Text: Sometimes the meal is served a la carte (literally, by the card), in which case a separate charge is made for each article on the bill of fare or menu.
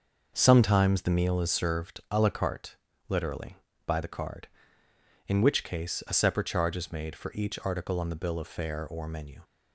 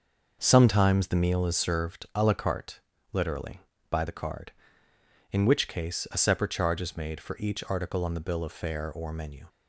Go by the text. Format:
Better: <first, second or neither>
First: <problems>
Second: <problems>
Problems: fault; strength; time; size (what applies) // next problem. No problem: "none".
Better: neither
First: starts louder than the rest; until 1.3 s; 6 dB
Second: starts louder than the rest; until 1.4 s; 6 dB